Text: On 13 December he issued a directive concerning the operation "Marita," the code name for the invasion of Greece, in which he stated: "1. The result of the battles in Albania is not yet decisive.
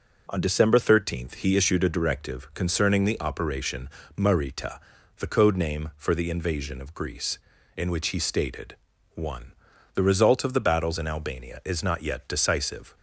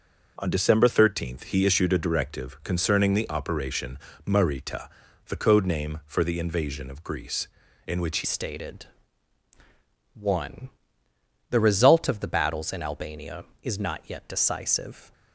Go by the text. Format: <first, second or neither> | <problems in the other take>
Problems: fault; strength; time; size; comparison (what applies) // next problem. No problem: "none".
first | pauses between "operation" and "Marita"; slight; at 3.9 s; 0.28 s long; slight in the first // changes voice at "stated"; from 8.2 s on; 6.9 s long